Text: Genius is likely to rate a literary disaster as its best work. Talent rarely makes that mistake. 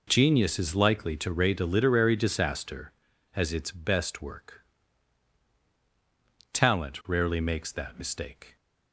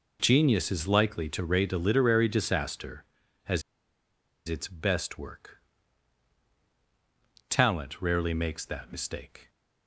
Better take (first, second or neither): first